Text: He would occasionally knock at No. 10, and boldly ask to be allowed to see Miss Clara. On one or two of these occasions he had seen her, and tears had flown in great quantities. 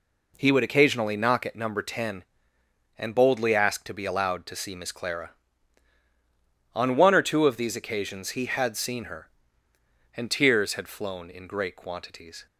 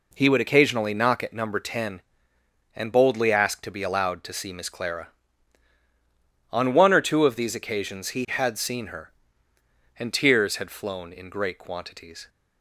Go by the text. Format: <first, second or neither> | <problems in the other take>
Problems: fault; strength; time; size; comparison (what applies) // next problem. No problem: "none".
neither | none